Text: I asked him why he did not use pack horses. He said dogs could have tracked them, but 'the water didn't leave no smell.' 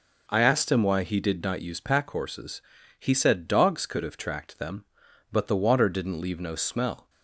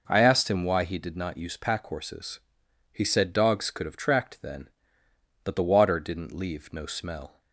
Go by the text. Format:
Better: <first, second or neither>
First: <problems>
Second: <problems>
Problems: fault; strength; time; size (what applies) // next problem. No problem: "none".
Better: first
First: none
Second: says "then" for "them"; at 4.4 s